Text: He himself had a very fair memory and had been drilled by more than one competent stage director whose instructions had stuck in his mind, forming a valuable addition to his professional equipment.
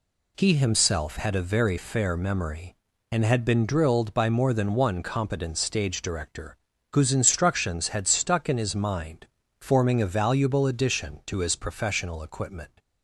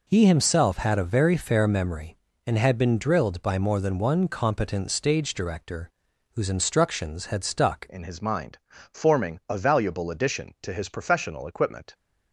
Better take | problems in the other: first | pauses between "director" and "whose"; at 5.9 s; 0.44 s long; slight in the first // changes voice at "in"; from 7.8 s on; 4.1 s long

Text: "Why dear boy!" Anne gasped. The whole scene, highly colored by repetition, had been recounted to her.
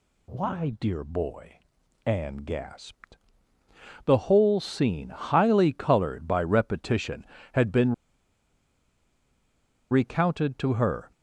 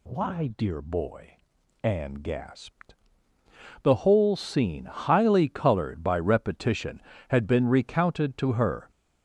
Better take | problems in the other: second | pauses between "been" and "recounted"; strong; at 7.9 s; 1.9 s long

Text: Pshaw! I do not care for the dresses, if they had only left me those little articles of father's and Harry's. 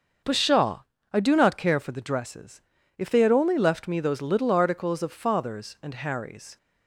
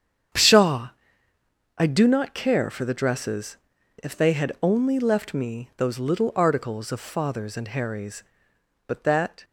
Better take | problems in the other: first | starts louder than the rest; strong; until 2.2 s; 8.5 dB; also in the first // goes on to say "But that"; from 8.8 s on; 0.58 s long

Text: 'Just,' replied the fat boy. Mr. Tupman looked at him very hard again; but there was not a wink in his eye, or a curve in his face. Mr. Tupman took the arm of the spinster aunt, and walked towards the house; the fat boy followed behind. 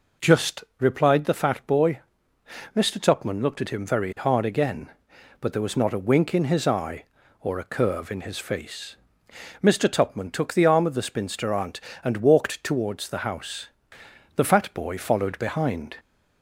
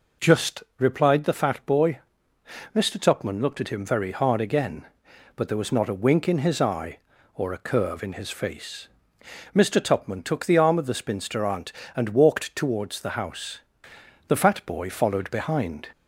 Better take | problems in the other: neither | none

